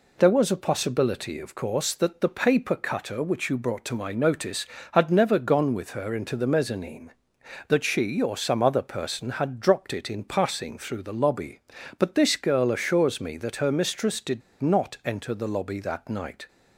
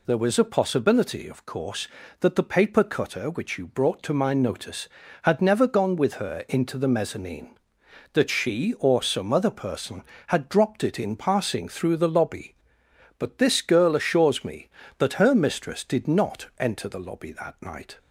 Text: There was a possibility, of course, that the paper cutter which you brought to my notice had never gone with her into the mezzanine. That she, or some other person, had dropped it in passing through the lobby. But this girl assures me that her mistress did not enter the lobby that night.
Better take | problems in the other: second | pauses between "did" and "not"; slight; at 14.4 s; 0.20 s long

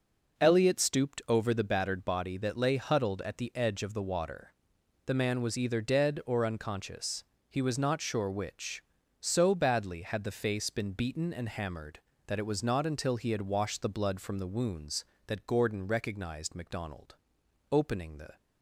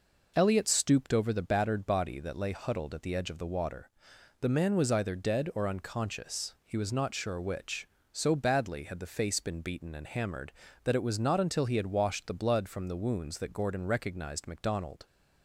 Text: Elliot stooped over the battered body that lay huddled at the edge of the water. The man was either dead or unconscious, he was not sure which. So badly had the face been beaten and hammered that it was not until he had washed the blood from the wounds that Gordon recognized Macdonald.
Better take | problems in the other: second | goes on to say "Opening the"; noticeable; from 17.7 s on; 0.64 s long

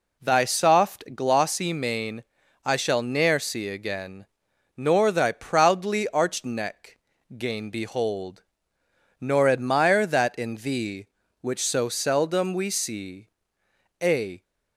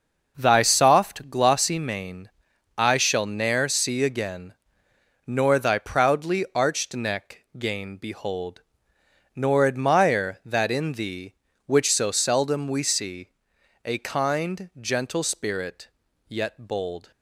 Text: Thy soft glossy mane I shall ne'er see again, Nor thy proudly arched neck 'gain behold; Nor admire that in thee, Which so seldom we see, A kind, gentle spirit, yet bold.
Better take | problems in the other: second | pauses between "mane" and "I"; at 2.2 s; 0.40 s long; noticeable in the second // pauses between "neck" and "gain"; at 6.9 s; 0.40 s long // stops before "kind gentle spirit yet bold"; at 14.4 s

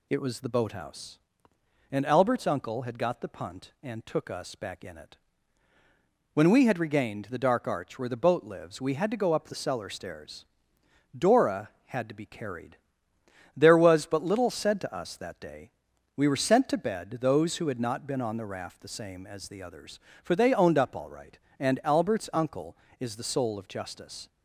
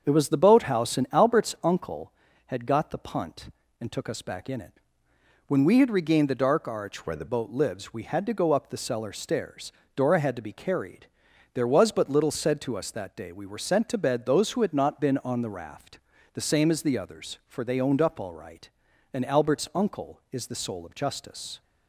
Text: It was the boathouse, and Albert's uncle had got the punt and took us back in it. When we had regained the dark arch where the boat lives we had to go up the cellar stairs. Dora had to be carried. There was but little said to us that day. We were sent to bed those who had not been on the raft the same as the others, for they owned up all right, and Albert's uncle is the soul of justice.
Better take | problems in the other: first | starts louder than the rest; strong; until 1.0 s; 7 dB // changes voice from "where" to "the"; from 7.0 to 7.2 s; 0.2 s long // pauses between "raft" and "the"; slight; at 15.9 s; 0.36 s long

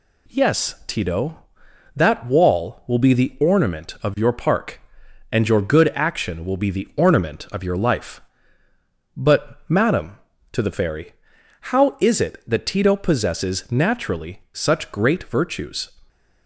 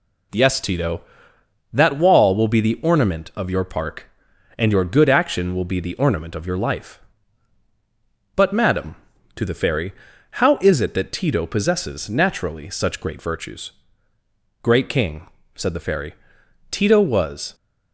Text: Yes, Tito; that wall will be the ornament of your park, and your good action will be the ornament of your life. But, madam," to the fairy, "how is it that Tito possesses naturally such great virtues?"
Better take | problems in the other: first | goes on to say "Great king said the fairy Tito was"; strong; from 14.6 s on; 2.9 s long

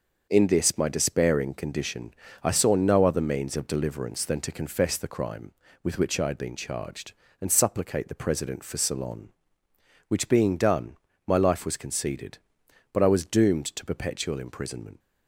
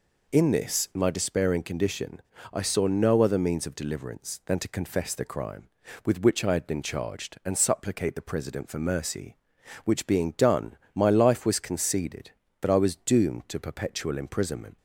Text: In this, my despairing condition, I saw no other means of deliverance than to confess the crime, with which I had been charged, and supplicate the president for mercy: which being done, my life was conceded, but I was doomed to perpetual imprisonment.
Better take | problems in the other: second | starts louder than the rest; until 1.3 s; 6 dB // says "ceylon" for "mercy"; at 8.7 s

